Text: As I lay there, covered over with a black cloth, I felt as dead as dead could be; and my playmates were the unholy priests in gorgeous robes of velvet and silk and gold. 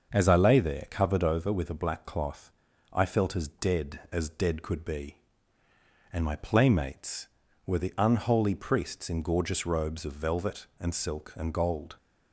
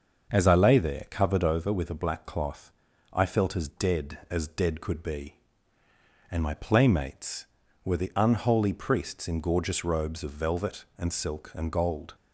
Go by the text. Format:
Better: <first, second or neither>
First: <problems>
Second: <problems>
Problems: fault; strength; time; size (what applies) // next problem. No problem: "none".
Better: neither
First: starts louder than the rest; until 1.1 s; 6.5 dB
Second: starts louder than the rest; until 1.3 s; 6.5 dB